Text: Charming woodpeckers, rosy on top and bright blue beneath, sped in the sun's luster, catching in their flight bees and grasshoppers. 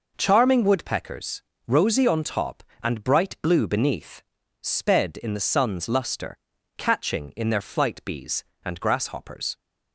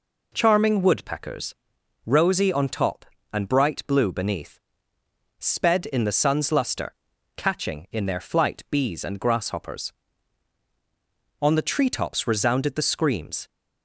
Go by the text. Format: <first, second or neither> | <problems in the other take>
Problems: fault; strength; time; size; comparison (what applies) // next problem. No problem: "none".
first | goes on to say "On the treetops resounded the screams"; strong; from 11.4 s on; 2.0 s long